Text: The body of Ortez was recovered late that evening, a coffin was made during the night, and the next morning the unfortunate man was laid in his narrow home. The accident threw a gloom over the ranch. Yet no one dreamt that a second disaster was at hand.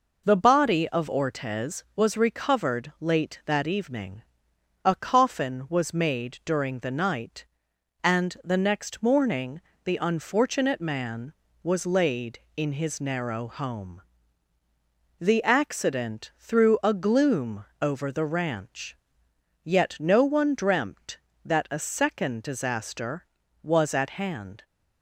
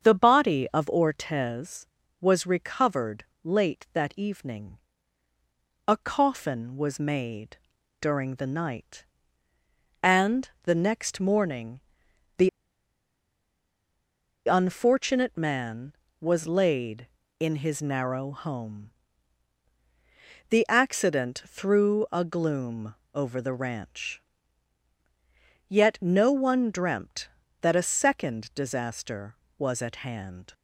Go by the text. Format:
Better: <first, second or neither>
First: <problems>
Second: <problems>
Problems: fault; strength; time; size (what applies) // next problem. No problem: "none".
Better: first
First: pauses between "morning" and "the"; slight; at 9.6 s; 0.22 s long // pauses between "gloom" and "over"; slight; at 17.6 s; 0.16 s long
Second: starts louder than the rest; strong; until 1.1 s; 7 dB // pauses between "recovered" and "late"; slight; at 3.2 s; 0.22 s long // pauses between "made" and "during"; at 7.5 s; 0.42 s long // pauses between "and" and "the"; slight; at 10.4 s; 0.16 s long // pauses between "morning" and "the"; noticeable; at 11.7 s; 0.58 s long // pauses between "the" and "unfortunate"; strong; at 12.4 s; 1.9 s long // pauses between "gloom" and "over"; slight; at 22.9 s; 0.18 s long